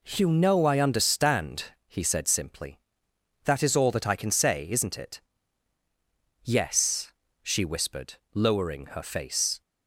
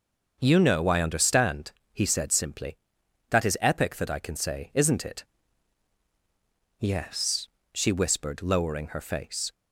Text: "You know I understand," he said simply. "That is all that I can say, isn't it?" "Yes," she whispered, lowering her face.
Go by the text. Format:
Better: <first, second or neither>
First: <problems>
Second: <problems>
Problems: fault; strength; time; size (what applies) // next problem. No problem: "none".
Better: first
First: none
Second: starts louder than the rest; until 1.4 s; 6.5 dB // says "epic" for "all"; at 3.6 s